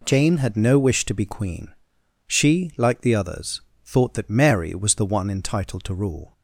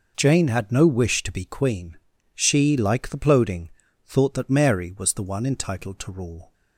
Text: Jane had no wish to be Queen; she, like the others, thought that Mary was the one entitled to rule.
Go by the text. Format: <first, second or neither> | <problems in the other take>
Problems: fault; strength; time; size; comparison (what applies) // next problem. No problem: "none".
first | says "ploding" for "others"; at 3.1 s